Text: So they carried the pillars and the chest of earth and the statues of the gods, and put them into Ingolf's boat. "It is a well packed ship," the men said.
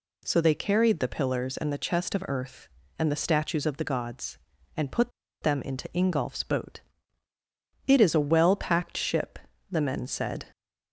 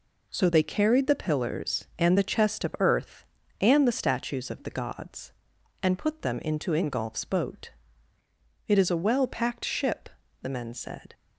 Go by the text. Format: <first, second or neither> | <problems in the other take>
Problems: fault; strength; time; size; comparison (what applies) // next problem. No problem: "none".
second | pauses between "put" and "them"; slight; at 5.1 s; 0.31 s long